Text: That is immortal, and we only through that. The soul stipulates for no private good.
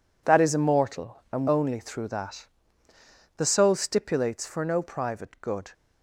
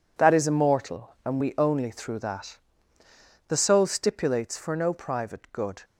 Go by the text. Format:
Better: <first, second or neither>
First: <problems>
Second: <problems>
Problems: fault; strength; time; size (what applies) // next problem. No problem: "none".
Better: second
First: skips "we"; at 1.4 s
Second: none